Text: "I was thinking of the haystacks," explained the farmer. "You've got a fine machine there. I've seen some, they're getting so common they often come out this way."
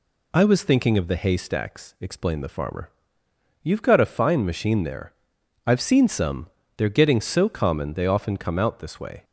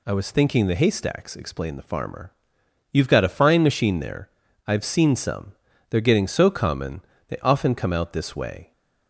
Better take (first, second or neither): first